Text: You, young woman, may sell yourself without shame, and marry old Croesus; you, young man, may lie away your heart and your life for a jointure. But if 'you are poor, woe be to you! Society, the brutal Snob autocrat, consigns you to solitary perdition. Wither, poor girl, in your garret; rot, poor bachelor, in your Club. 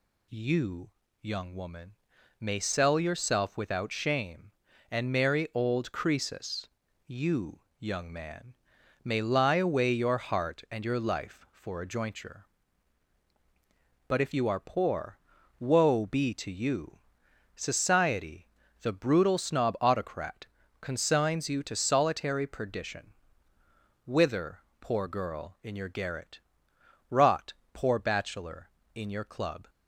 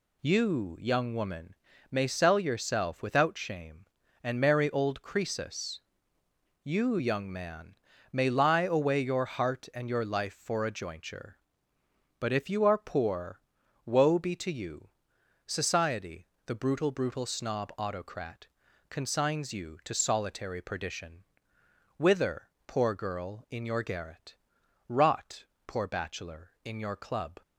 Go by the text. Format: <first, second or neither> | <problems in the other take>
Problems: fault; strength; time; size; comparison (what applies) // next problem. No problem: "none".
first | says "brutal" twice; at 16.9 s